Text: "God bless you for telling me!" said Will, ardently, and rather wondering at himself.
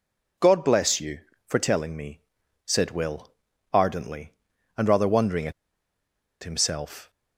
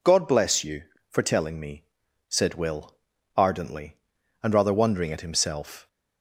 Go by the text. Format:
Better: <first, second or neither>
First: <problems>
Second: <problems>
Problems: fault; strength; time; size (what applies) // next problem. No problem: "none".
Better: second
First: pauses between "at" and "himself"; noticeable; at 5.5 s; 0.91 s long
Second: none